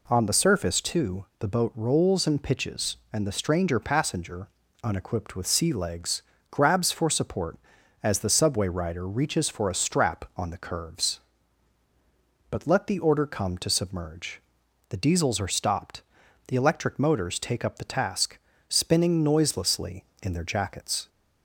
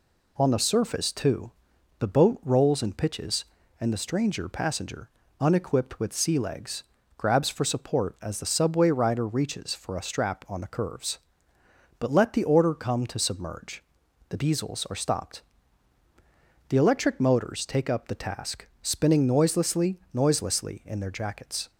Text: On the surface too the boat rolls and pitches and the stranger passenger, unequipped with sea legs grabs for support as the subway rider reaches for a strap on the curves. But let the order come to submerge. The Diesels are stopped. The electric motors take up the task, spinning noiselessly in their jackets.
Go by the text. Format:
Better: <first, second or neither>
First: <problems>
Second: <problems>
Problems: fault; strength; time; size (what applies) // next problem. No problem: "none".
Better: first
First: pauses between "too" and "the"; slight; at 1.2 s; 0.16 s long // pauses between "legs" and "grabs"; slight; at 6.2 s; 0.30 s long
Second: pauses between "too" and "the"; noticeable; at 1.5 s; 0.48 s long // pauses between "legs" and "grabs"; slight; at 6.8 s; 0.34 s long // says "noiselessly" twice; at 20.1 s